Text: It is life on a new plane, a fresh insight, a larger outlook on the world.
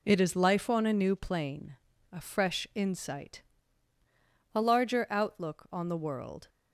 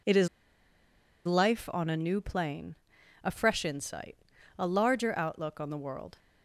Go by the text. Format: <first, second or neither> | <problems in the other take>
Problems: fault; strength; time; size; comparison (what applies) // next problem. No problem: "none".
first | pauses between "is" and "life"; at 0.2 s; 1.0 s long